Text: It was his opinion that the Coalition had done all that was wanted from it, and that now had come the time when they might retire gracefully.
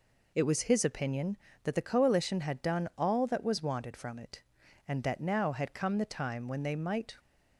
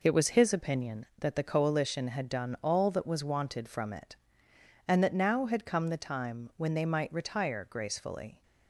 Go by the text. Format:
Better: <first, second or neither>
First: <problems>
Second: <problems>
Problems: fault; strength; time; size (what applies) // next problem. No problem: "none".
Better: second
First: stops before "retire gracefully"; at 7.1 s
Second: none